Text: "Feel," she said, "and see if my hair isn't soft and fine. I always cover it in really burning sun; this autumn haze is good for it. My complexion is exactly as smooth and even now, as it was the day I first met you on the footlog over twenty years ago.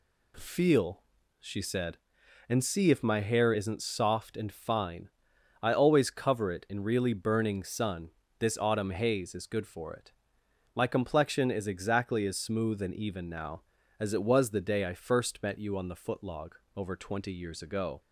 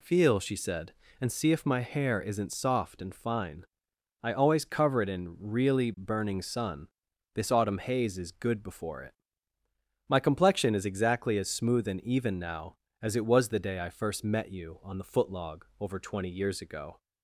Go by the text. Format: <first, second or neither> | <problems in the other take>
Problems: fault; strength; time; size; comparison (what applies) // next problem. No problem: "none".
first | says "before" for "for"; at 8.6 s // pauses between "footlog" and "over"; slight; at 15.6 s; 0.18 s long; slight in the first